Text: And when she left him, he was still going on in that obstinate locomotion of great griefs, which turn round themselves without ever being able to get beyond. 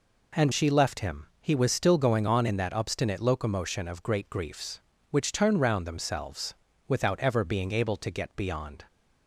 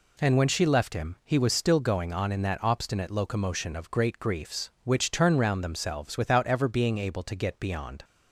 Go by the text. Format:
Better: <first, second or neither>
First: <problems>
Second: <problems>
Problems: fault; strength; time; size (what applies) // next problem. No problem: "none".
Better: second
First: skips "when"; at 0.5 s // pauses between "themselves" and "without"; slight; at 6.5 s; 0.34 s long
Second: none